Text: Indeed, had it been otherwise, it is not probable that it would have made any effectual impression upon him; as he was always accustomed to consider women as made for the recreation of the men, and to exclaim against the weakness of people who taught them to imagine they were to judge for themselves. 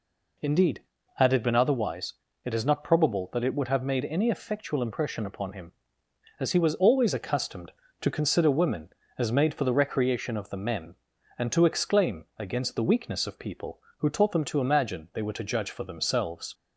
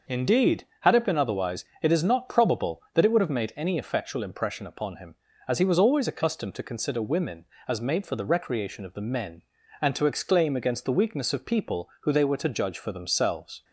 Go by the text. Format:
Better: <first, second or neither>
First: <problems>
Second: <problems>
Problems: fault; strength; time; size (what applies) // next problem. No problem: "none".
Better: first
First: none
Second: starts louder than the rest; noticeable; until 1.2 s; 6 dB // skips "taught them to imagine"; at 12.1 s